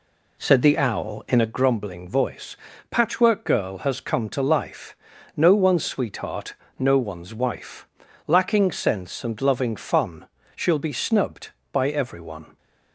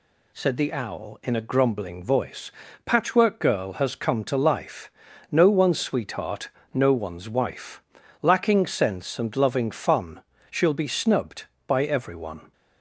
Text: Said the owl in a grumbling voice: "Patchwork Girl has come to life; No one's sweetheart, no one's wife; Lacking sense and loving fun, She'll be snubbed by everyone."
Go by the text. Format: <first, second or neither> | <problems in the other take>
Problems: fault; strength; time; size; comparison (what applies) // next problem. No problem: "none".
second | starts louder than the rest; slight; until 1.6 s; 2 dB